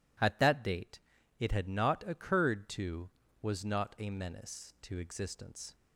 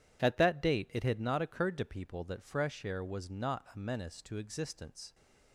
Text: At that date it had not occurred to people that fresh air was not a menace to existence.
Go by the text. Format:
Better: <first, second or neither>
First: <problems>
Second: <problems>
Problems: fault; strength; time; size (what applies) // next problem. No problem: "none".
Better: second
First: pauses between "date" and "it"; at 0.9 s; 0.40 s long // skips "people that fresh air"; at 3.2 s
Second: none